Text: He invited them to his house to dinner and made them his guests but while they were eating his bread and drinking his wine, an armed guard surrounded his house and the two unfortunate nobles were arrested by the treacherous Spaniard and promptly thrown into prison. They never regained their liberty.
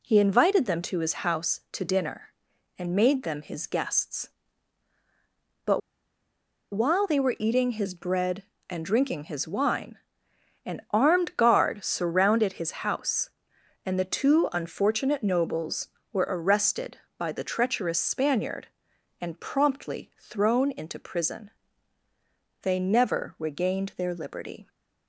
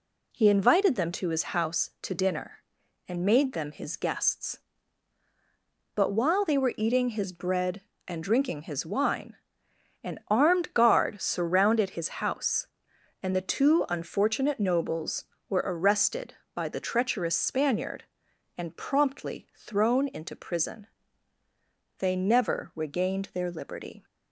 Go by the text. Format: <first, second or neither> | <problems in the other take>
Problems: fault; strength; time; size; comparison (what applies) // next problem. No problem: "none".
second | pauses between "but" and "while"; noticeable; at 5.8 s; 0.94 s long // pauses between "his" and "house"; slight; at 12.7 s; 0.16 s long; slight in the second